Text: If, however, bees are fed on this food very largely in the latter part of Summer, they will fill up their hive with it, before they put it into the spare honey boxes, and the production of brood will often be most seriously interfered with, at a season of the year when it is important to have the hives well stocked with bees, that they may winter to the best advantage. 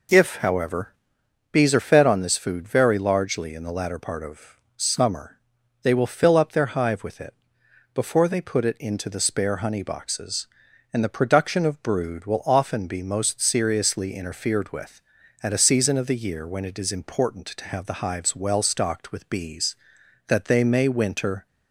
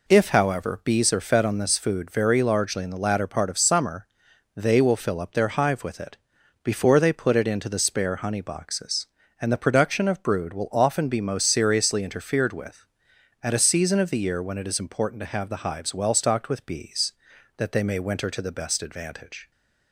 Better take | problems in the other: second | pauses between "of" and "Summer"; slight; at 4.5 s; 0.20 s long // stops before "to the best advantage"; at 21.4 s

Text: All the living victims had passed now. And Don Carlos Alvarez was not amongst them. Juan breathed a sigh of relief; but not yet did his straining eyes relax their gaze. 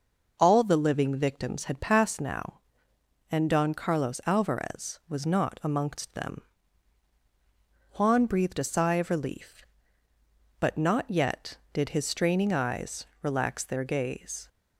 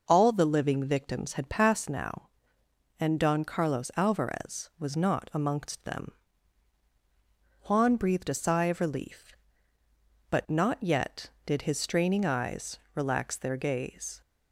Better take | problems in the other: neither | pauses between "eyes" and "relax"; slight; the same in both

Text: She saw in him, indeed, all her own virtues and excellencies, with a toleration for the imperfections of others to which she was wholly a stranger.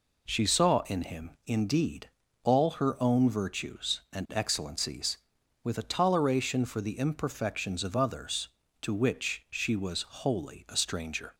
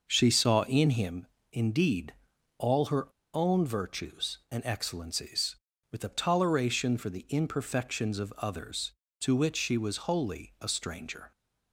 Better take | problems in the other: first | pauses between "her" and "own"; slight; at 3.0 s; 0.25 s long

